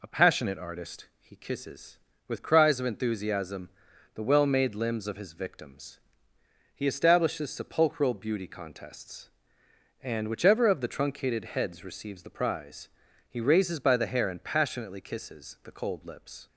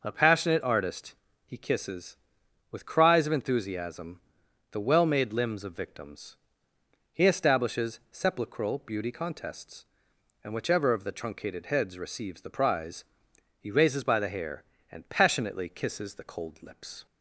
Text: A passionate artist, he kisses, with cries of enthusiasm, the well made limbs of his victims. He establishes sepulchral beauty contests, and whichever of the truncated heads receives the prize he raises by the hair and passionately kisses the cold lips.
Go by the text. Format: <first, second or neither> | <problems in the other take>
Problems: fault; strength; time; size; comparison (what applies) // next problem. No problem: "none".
first | skips "his"; at 5.7 s // pauses between "prize" and "he"; noticeable; at 13.0 s; 0.56 s long; also in the first